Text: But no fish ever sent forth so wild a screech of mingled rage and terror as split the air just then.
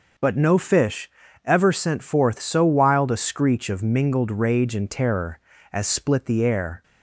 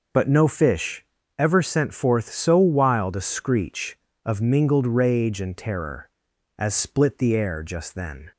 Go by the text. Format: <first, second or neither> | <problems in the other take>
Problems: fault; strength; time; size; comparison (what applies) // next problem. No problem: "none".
second | pauses between "fish" and "ever"; slight; at 1.1 s; 0.34 s long; slight in the second // stops before "just then"; at 6.8 s